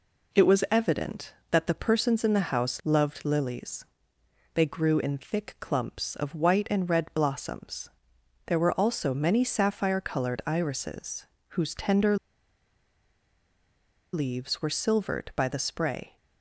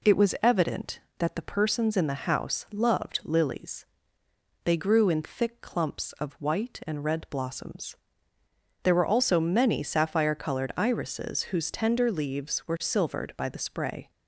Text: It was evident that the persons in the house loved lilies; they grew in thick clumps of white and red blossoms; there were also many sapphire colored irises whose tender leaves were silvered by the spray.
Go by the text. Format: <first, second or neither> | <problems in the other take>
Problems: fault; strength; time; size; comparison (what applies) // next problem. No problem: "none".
second | pauses between "irises" and "whose"; slight; at 11.2 s; 0.30 s long // pauses between "tender" and "leaves"; strong; at 12.1 s; 1.9 s long